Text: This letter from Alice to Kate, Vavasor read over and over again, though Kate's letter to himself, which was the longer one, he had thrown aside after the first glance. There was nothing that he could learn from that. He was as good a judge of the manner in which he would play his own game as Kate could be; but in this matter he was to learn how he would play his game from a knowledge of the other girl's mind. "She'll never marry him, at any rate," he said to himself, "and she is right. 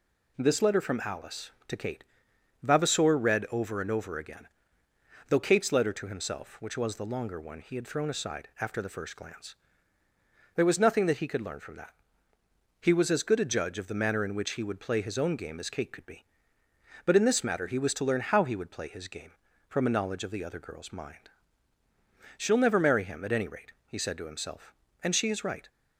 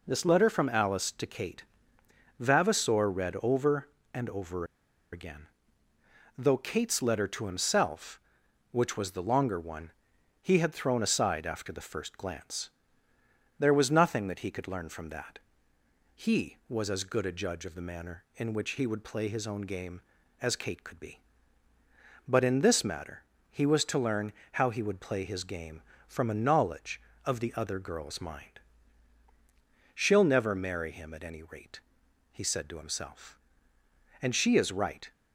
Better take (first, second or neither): first